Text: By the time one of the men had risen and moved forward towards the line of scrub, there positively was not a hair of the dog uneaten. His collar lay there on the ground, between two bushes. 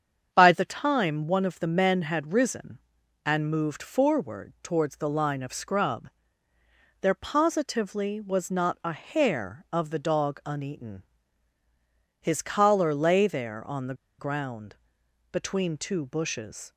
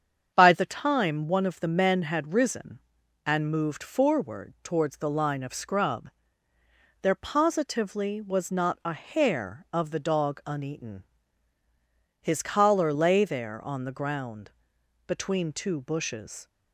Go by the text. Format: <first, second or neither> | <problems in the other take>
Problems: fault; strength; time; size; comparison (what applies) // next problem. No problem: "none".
second | starts louder than the rest; strong; until 1.3 s; 7.5 dB; strong in the second // pauses between "the" and "ground"; slight; at 13.9 s; 0.24 s long